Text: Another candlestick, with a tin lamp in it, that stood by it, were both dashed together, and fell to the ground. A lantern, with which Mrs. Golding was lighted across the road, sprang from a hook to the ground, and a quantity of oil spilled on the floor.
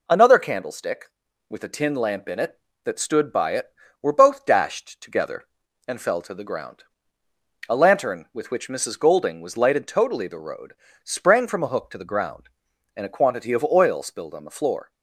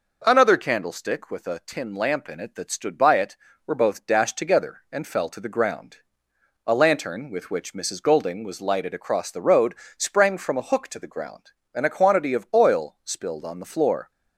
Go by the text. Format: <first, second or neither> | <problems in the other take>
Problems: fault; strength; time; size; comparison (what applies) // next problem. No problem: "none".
second | says "totally" for "across"; at 9.8 s